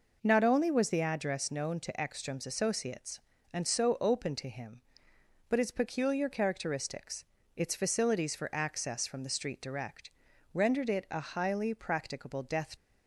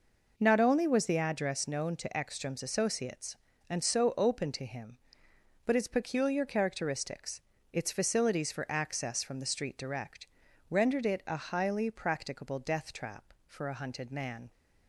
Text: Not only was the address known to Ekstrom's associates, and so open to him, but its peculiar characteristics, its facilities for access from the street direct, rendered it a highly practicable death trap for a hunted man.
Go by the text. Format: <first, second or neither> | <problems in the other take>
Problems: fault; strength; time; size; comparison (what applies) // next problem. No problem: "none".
second | stops before "trap for a hunted man"; at 12.7 s